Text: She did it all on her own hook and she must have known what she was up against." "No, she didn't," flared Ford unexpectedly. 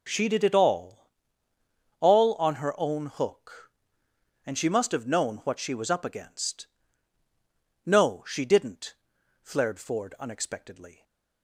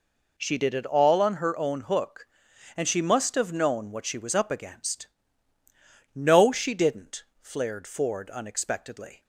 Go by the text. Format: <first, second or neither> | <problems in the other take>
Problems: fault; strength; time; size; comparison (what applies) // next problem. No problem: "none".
second | says "all" twice; at 1.9 s